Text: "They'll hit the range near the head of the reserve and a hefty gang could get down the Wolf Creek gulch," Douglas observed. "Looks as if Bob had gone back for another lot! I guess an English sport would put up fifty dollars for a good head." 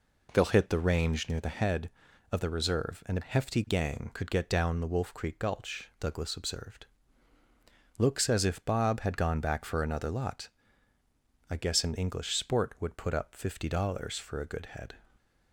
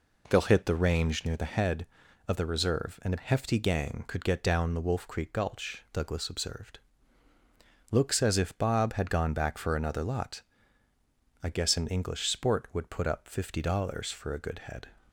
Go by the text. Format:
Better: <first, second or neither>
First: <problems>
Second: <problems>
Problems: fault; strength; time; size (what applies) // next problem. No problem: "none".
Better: neither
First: none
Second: none